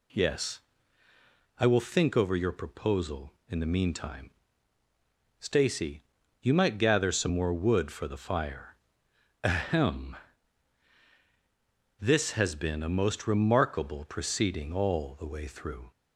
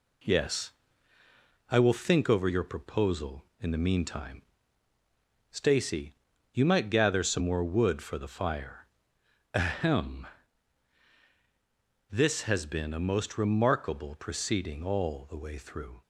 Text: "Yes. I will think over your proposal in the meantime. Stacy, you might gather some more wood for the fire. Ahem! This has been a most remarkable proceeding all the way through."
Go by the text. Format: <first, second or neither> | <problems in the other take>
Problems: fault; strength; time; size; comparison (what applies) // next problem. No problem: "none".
first | gets quieter; throughout; 3.5 dB